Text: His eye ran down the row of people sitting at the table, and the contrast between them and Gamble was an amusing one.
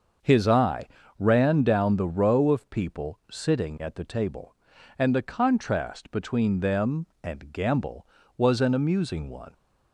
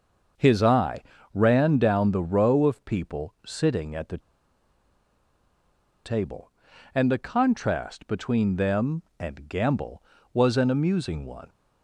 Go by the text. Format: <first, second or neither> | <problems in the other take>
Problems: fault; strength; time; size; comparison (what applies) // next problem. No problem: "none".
first | starts louder than the rest; until 1.6 s; 6.5 dB; also in the first // pauses between "eye" and "ran"; slight; at 1.0 s; 0.32 s long; slight in the first // pauses between "the" and "table"; strong; at 4.1 s; 1.8 s long